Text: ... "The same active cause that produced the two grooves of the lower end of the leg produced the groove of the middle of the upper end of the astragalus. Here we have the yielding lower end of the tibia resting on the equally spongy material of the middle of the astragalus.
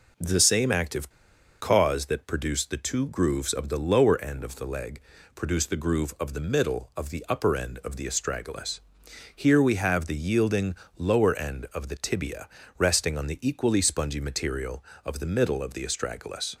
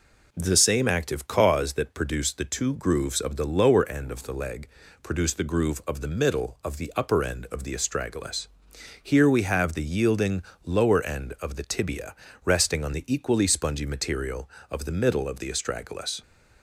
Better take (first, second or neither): second